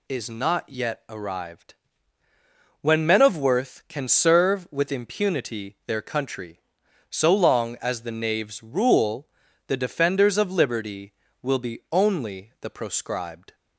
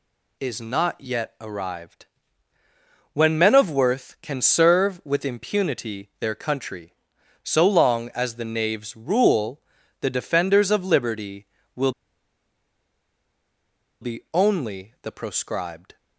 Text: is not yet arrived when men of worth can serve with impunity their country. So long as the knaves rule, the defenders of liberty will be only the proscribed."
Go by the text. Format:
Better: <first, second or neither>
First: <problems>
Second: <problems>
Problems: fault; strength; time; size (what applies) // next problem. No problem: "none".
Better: first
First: pauses between "arrived" and "when"; at 1.7 s; 1.0 s long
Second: pauses between "arrived" and "when"; at 2.0 s; 1.0 s long // pauses between "will" and "be"; strong; at 11.8 s; 2.1 s long